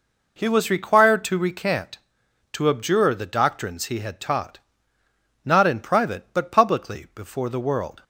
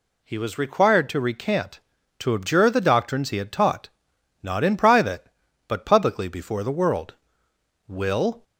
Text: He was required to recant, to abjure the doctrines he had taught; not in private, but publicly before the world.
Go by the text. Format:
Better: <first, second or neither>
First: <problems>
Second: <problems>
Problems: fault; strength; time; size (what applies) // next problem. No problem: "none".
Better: first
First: none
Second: goes on to say "Will"; from 7.8 s on; 0.54 s long